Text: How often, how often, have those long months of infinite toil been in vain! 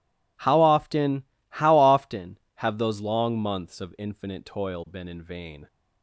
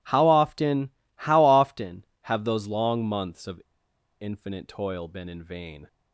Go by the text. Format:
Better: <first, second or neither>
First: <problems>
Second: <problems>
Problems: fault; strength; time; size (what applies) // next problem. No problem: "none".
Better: first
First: none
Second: pauses between "of" and "infinite"; noticeable; at 3.6 s; 0.60 s long